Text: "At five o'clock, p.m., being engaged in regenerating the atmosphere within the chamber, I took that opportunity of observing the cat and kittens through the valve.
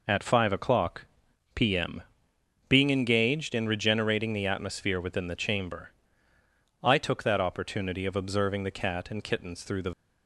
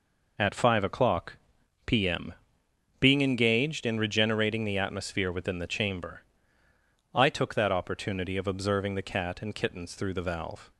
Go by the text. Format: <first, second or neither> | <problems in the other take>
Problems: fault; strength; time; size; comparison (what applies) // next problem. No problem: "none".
second | stops before "valve"; at 9.9 s